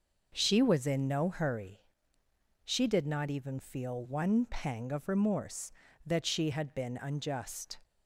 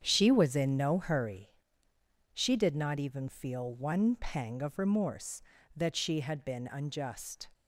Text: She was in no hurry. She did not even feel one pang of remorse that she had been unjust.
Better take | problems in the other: first | gets quieter; strong; throughout; 10.5 dB

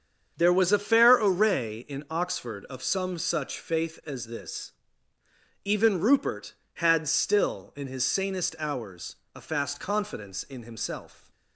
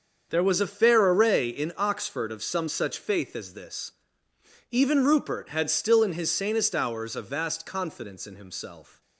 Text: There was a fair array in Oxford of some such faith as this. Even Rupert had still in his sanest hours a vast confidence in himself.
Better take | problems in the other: second | starts louder than the rest; strong; until 1.3 s; 7.5 dB; also in the second // pauses between "hours" and "a"; slight; at 9.1 s; 0.20 s long // says "fast" for "vast"; at 9.4 s

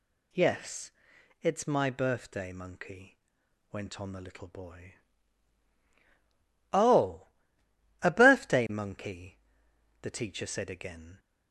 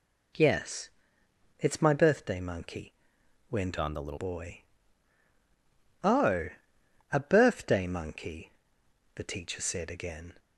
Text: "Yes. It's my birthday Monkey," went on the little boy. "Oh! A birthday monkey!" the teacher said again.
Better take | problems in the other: first | changes voice from "on" to "little"; from 3.8 to 4.1 s; 0.3 s long

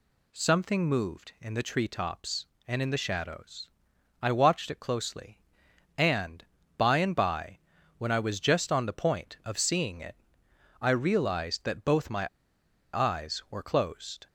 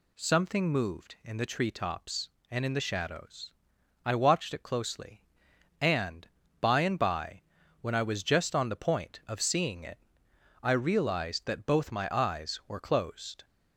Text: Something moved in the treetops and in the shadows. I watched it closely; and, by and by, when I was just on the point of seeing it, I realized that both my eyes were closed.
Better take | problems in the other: second | pauses between "my" and "eyes"; noticeable; at 12.2 s; 0.66 s long

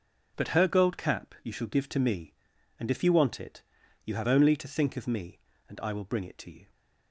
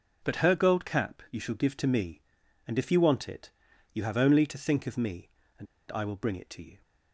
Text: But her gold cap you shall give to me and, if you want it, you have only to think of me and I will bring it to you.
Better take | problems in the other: first | pauses between "and" and "I"; slight; at 5.6 s; 0.26 s long

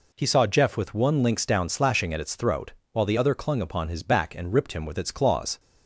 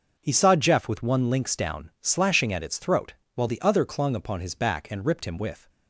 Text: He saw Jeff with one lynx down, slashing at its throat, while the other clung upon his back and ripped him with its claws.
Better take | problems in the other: first | starts louder than the rest; until 1.2 s; 6 dB // stops before "its claws"; at 5.6 s

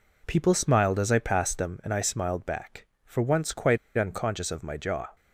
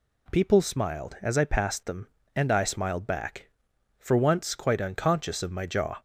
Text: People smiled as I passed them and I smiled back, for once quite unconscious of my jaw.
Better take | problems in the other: second | pauses between "quite" and "unconscious"; slight; at 3.7 s; 0.20 s long

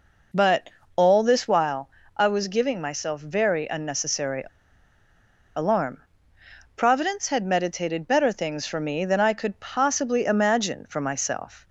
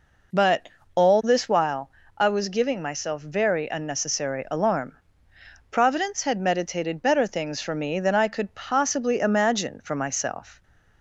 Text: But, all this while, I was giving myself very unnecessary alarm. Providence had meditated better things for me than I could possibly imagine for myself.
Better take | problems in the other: second | pauses between "unnecessary" and "alarm"; at 4.4 s; 1.1 s long

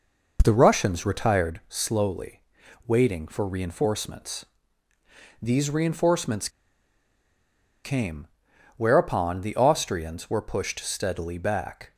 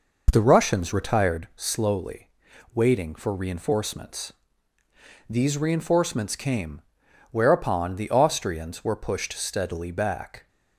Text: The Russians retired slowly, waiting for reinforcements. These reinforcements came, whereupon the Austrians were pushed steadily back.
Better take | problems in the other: second | pauses between "reinforcements" and "came"; strong; at 6.4 s; 1.3 s long

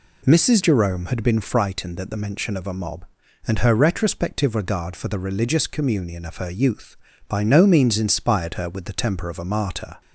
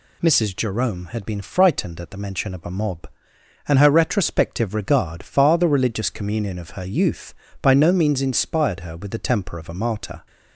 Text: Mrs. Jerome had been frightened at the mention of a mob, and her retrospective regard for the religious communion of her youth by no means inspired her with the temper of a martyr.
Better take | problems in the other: first | says "far" for "for"; at 5.2 s

